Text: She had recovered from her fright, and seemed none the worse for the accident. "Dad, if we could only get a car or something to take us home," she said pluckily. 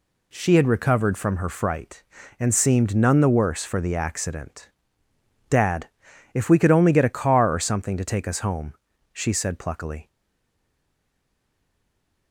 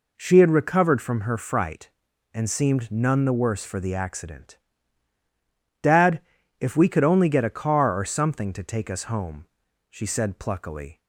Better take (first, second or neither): second